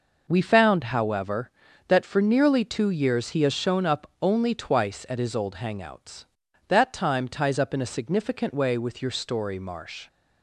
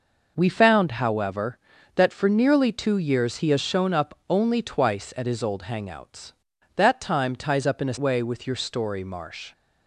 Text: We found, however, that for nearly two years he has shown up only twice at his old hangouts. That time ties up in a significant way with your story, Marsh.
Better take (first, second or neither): first